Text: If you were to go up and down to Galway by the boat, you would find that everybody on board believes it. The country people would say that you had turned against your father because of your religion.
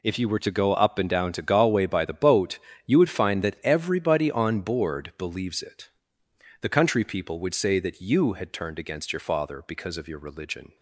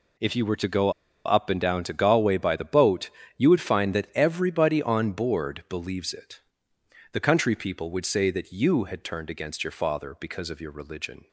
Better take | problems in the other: first | pauses between "go" and "up"; slight; at 0.9 s; 0.34 s long

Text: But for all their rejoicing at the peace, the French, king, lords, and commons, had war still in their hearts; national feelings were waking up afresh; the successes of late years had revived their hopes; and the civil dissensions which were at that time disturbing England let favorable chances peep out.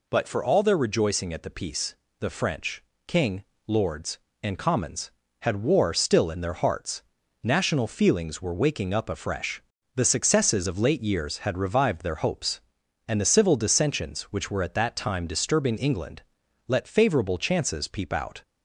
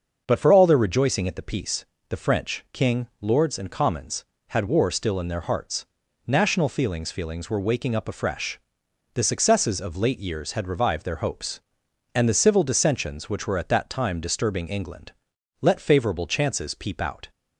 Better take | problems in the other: first | starts louder than the rest; until 1.2 s; 6 dB // says "feelings" twice; at 7.0 s // pauses between "England" and "let"; noticeable; at 15.1 s; 0.48 s long; noticeable in the first

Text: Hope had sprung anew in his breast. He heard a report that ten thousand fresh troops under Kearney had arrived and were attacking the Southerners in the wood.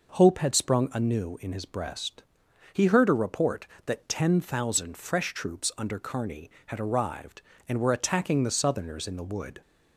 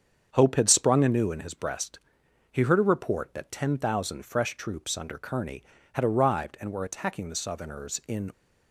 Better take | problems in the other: first | starts louder than the rest; strong; until 1.3 s; 7.5 dB // stops before "the wood"; at 8.3 s

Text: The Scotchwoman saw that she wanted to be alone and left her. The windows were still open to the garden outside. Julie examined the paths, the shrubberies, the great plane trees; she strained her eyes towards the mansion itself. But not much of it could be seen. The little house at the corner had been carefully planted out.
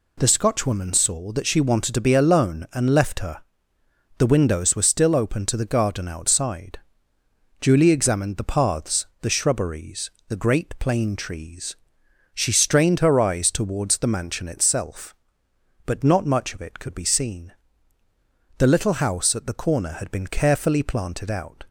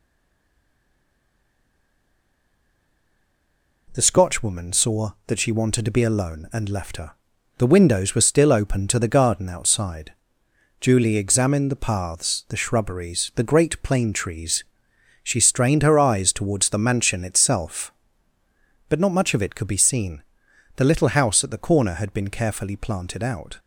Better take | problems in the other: first | stays silent before the first word; strong; until 3.8 s; 3.8 s long

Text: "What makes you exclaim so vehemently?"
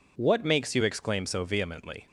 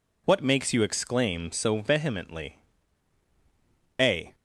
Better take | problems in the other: first | goes on to say "A"; slight; from 4.0 s on; 0.34 s long

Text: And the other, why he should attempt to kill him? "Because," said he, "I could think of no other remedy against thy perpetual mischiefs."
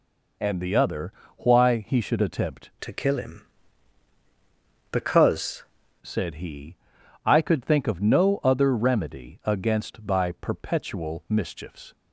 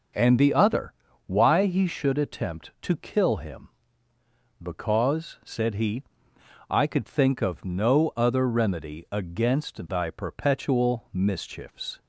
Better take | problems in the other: second | changes voice from "to" to "Because"; from 2.8 to 5.6 s; 2.8 s long

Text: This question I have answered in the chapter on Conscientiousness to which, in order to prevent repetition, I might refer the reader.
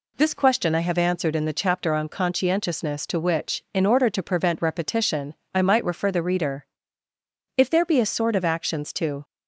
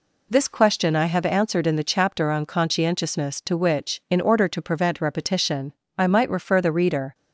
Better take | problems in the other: second | goes on to say "If there be a sort of actions to"; from 7.5 s on; 1.6 s long

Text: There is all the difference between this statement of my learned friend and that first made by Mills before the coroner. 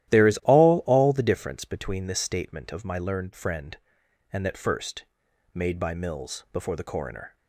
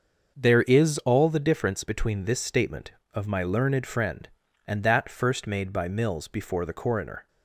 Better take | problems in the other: second | starts louder than the rest; strong; until 1.1 s; 13.5 dB; also in the second // says "all" twice; at 0.8 s // pauses between "first" and "made"; noticeable; at 5.0 s; 0.50 s long

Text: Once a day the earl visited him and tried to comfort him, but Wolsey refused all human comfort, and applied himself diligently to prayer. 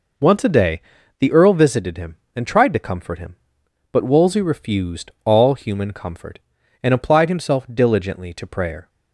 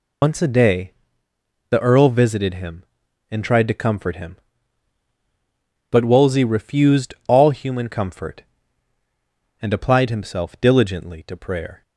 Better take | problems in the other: first | loses the start of "Once"; at 0.2 s; 85 ms // pauses between "day" and "the"; noticeable; at 0.9 s; 0.78 s long; also in the first // pauses between "refused" and "all"; slight; at 7.1 s; 0.16 s long

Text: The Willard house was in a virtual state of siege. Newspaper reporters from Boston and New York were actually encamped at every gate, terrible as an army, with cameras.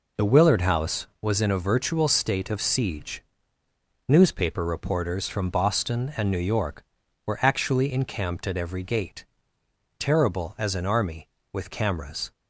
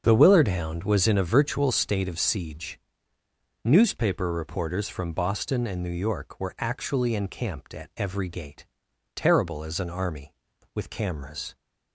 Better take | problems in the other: first | starts louder than the rest; until 1.0 s; 7 dB // says "hound" for "house"; at 0.4 s

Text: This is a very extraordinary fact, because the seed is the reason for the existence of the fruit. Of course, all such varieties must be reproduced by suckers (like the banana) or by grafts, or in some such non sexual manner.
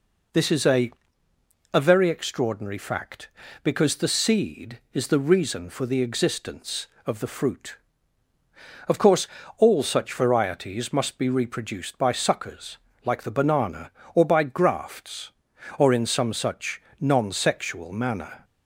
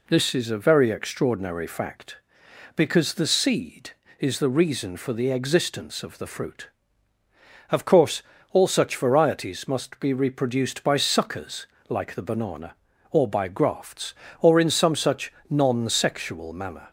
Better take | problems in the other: second | says "a" twice; at 1.7 s // pauses between "such" and "non"; slight; at 16.7 s; 0.20 s long; slight in the second

